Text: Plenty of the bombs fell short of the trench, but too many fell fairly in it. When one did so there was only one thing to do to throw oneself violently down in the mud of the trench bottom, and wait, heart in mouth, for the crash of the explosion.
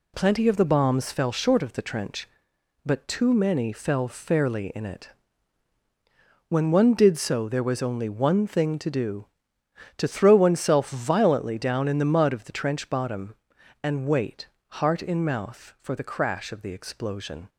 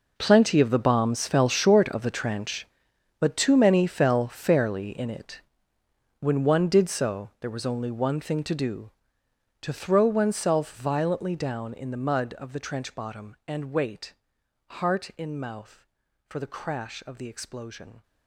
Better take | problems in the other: first | gets quieter; strong; throughout; 15 dB

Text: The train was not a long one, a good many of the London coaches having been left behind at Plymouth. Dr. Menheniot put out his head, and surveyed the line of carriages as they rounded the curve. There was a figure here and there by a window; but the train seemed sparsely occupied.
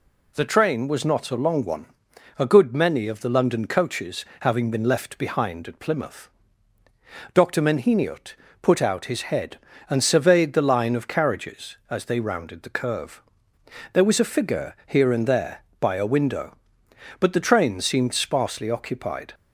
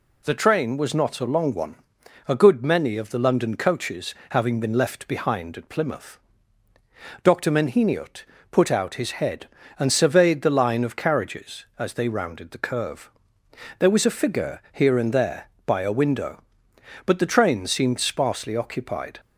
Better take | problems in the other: neither | pauses between "coaches" and "having"; slight; the same in both // pauses between "Menheniot" and "put"; slight; the same in both

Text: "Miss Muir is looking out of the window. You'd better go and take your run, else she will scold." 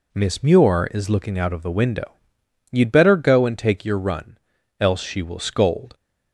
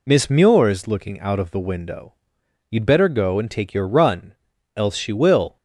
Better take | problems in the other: first | stops before "scold"; at 5.5 s

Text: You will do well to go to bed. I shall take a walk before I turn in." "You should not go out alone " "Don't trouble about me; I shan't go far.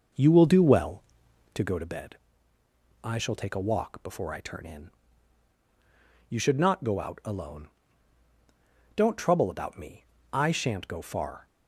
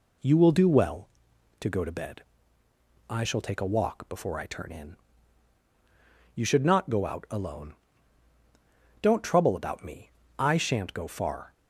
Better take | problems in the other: second | starts louder than the rest; noticeable; until 1.7 s; 6 dB

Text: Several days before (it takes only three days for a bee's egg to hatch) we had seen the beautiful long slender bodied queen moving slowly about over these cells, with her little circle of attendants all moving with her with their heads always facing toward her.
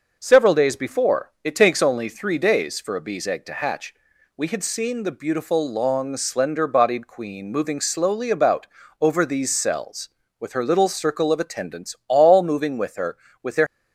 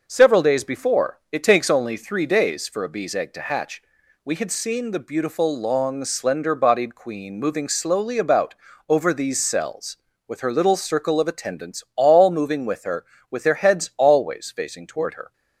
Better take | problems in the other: second | pauses between "about" and "over"; slight; at 8.6 s; 0.34 s long; slight in the second // stops before "heads always facing toward her"; at 13.6 s

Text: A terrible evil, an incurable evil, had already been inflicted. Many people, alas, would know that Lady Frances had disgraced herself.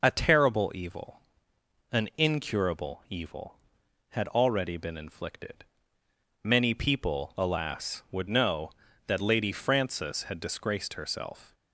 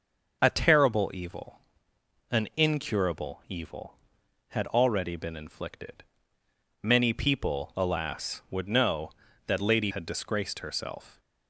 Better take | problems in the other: first | starts louder than the rest; noticeable; until 1.4 s; 6 dB // skips "Frances"; at 9.9 s

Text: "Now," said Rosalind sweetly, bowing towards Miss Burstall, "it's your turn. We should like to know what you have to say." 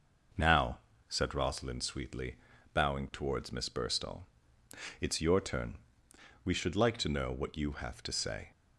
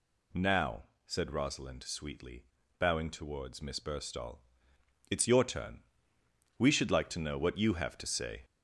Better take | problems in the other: first | gets louder; noticeable; throughout; 4 dB

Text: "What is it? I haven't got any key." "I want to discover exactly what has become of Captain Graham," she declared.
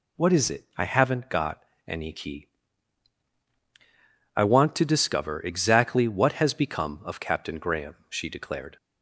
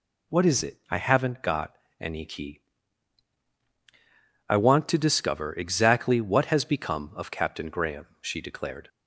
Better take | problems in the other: neither | pauses between "got" and "any"; slight; the same in both

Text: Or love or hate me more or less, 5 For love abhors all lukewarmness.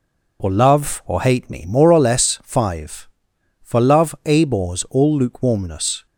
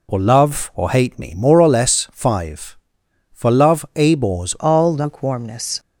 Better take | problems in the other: first | changes voice at "all"; from 4.5 s on; 1.2 s long

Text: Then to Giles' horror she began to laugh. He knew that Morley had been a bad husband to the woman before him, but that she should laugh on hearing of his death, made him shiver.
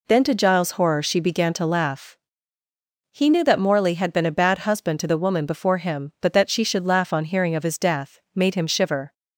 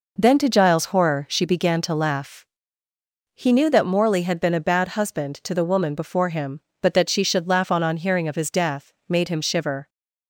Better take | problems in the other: first | says "on" twice; at 7.8 s

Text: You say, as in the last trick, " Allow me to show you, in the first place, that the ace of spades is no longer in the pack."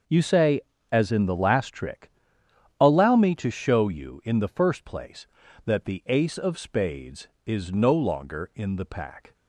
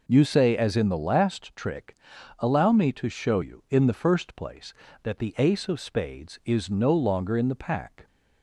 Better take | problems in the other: neither | none

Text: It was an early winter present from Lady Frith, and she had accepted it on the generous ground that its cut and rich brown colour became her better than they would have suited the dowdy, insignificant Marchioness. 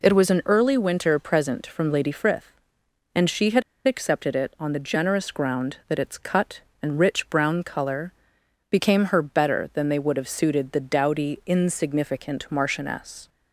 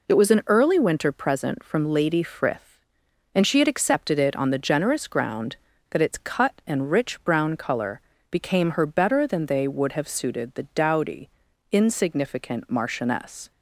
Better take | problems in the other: second | pauses between "had" and "accepted"; slight; at 3.6 s; 0.24 s long // pauses between "colour" and "became"; noticeable; at 8.1 s; 0.60 s long; slight in the second

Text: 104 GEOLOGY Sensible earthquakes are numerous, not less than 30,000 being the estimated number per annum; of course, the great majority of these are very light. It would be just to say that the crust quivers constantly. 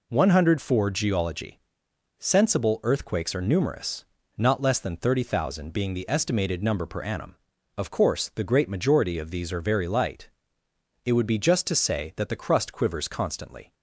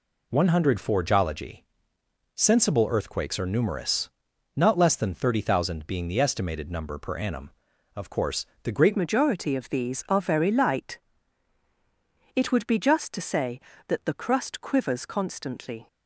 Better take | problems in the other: first | pauses between "GEOLOGY" and "Sensible"; noticeable; at 1.6 s; 0.70 s long; noticeable in the first // changes voice at "majority"; from 8.9 s on; 6.9 s long

